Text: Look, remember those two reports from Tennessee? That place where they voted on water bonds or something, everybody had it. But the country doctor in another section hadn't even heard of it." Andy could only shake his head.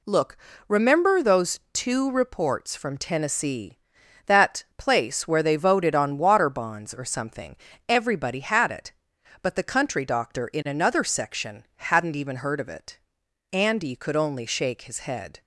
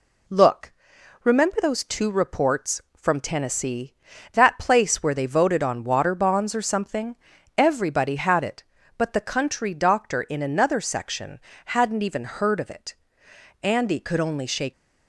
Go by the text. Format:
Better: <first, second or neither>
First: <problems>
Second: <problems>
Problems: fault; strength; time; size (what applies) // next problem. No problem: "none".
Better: first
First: none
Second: pauses between "section" and "hadn't"; slight; at 11.3 s; 0.28 s long // stops before "his head"; at 14.7 s